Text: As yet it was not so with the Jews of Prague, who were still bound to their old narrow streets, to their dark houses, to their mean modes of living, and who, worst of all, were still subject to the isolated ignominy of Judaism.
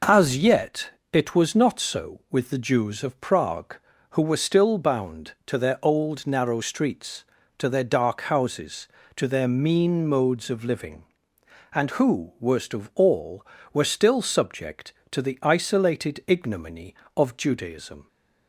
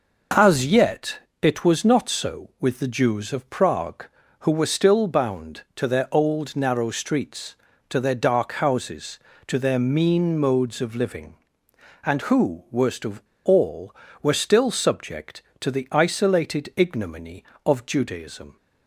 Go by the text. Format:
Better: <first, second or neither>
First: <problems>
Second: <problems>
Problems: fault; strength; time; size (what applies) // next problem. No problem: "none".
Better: first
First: pauses between "yet" and "it"; slight; at 0.8 s; 0.23 s long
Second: pauses between "yet" and "it"; slight; at 1.1 s; 0.24 s long // pauses between "of" and "all"; slight; at 13.2 s; 0.24 s long